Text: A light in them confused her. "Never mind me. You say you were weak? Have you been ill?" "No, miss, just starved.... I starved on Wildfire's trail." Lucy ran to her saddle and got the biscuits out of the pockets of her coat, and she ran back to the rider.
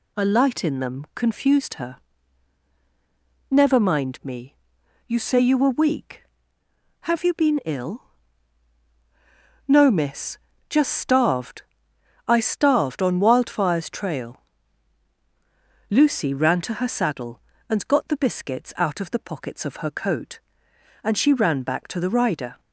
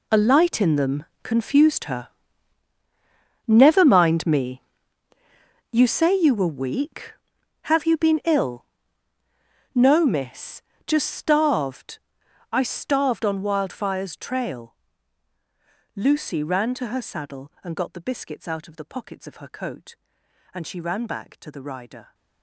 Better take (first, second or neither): first